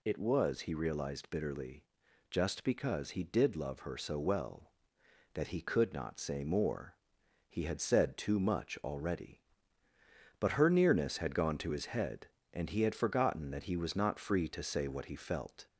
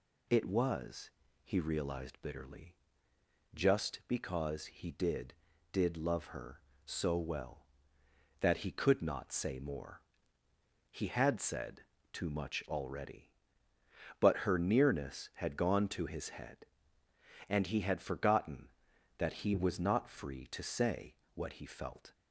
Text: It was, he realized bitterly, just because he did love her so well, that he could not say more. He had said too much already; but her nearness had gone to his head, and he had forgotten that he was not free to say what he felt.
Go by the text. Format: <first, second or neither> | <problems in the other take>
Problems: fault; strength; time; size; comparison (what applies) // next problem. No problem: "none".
first | says "did" twice; at 5.7 s // pauses between "said" and "too"; slight; at 11.8 s; 0.28 s long // pauses between "say" and "what"; slight; at 21.1 s; 0.18 s long